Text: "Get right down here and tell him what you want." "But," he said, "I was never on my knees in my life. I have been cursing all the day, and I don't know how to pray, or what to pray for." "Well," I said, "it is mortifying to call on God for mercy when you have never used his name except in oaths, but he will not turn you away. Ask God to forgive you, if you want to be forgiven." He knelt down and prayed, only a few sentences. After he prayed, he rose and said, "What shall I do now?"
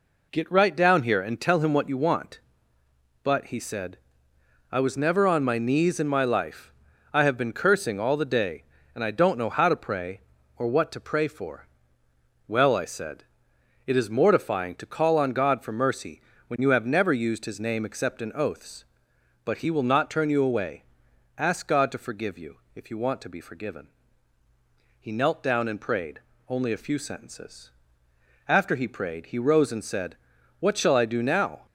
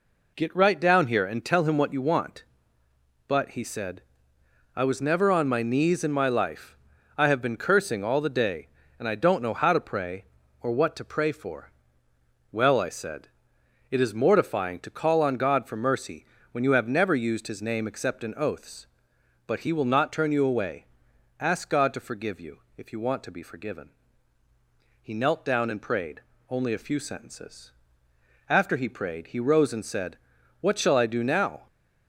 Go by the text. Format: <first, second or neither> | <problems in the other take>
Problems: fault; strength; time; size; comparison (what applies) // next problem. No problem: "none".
neither | pauses between "mercy" and "when"; slight; the same in both